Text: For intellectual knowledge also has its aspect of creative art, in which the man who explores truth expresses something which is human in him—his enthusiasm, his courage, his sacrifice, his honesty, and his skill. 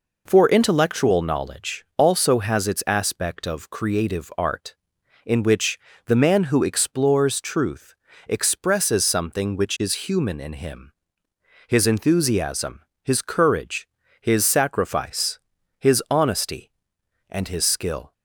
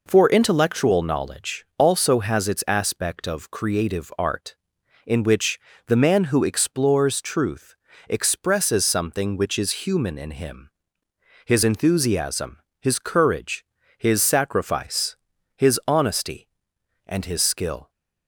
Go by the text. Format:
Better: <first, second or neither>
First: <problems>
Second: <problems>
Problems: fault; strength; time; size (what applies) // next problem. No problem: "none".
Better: neither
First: pauses between "which" and "the"; slight; at 5.7 s; 0.28 s long // pauses between "truth" and "expresses"; slight; at 7.9 s; 0.32 s long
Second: pauses between "which" and "the"; slight; at 5.5 s; 0.28 s long // pauses between "truth" and "expresses"; slight; at 7.7 s; 0.32 s long